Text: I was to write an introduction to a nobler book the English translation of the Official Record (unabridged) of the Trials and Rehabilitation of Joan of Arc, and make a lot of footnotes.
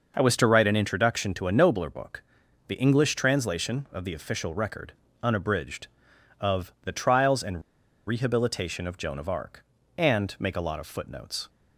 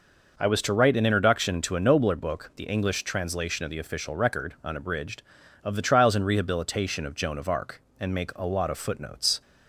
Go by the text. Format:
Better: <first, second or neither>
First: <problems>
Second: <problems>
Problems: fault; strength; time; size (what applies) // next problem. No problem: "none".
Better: second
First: pauses between "book" and "the"; at 2.2 s; 0.44 s long // pauses between "and" and "Rehabilitation"; at 7.6 s; 0.45 s long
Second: none